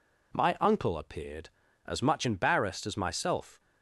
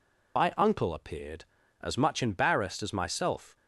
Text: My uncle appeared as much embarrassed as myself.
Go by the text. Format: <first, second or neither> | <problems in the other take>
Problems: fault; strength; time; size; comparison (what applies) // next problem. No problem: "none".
first | loses the start of "My"; at 0.3 s; 60 ms